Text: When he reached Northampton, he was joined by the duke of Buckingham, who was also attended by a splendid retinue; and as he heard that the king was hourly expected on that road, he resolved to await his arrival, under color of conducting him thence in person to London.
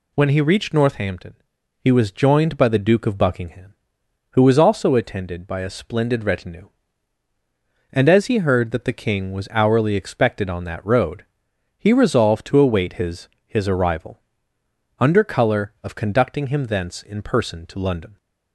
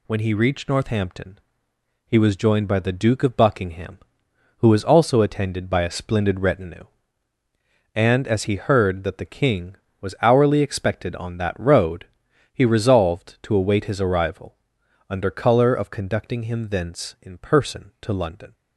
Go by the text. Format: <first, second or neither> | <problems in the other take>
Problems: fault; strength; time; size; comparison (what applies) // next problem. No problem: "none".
second | says "his" twice; at 13.4 s